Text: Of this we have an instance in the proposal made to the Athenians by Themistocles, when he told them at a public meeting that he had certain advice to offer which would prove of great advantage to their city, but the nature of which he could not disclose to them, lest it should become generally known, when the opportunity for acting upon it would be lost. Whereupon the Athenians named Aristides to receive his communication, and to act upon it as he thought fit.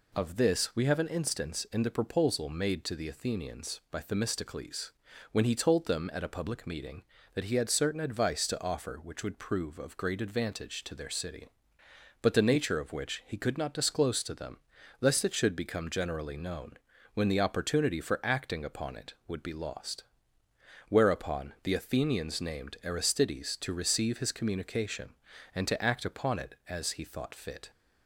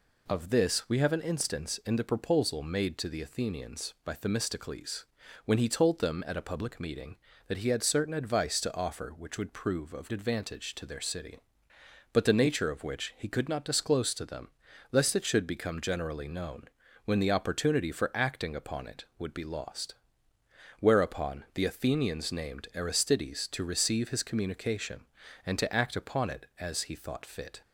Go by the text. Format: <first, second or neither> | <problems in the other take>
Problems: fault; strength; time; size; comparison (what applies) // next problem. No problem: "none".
first | skips "great"; at 10.1 s